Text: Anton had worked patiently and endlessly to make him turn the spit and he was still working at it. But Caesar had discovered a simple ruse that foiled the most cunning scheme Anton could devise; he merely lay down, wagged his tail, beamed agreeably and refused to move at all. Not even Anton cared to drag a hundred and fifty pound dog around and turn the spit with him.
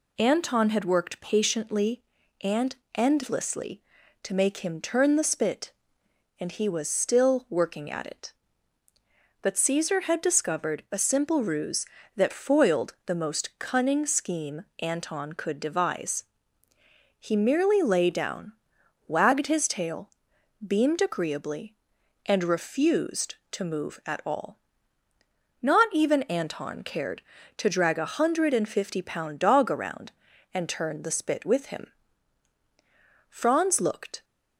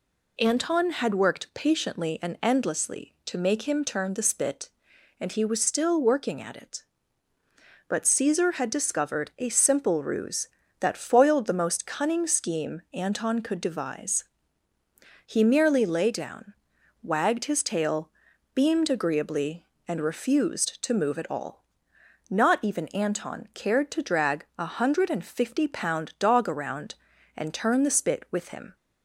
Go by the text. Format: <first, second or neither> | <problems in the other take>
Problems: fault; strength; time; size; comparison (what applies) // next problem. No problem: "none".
second | pauses between "and" and "endlessly"; slight; at 2.7 s; 0.18 s long // pauses between "scheme" and "Anton"; slight; at 14.6 s; 0.16 s long // goes on to say "Franz looked"; noticeable; from 33.2 s on; 0.94 s long